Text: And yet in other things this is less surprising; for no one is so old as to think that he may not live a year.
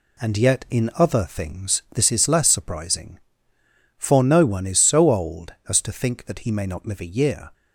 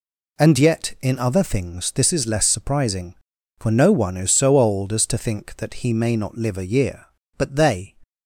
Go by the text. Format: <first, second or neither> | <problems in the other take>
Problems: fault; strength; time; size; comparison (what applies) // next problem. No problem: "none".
first | goes on to say "But they"; from 7.3 s on; 0.58 s long